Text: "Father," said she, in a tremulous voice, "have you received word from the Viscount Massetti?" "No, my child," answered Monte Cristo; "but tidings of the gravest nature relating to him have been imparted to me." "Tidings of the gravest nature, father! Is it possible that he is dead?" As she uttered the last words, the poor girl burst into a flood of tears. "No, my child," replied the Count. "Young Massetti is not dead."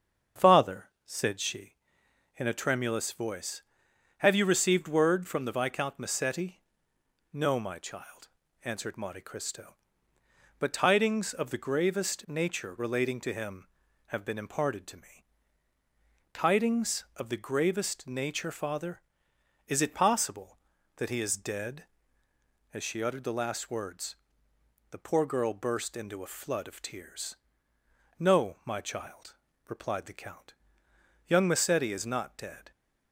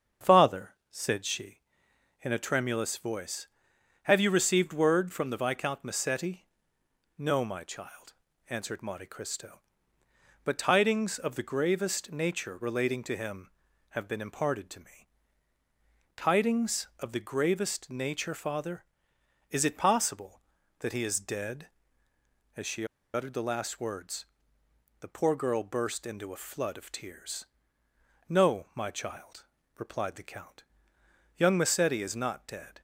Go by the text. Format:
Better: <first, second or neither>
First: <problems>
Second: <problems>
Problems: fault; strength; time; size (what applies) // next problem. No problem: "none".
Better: first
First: starts louder than the rest; strong; until 1.5 s; 7 dB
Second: starts louder than the rest; strong; until 1.3 s; 7 dB // pauses between "she" and "uttered"; slight; at 22.8 s; 0.28 s long